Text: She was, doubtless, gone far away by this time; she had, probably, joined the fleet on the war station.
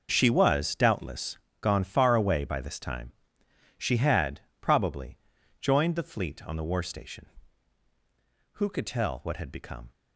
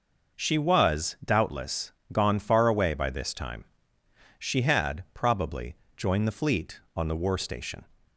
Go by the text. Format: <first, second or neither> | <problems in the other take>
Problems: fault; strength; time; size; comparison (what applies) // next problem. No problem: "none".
second | goes on to say "Who could tell what had become"; from 8.5 s on; 1.3 s long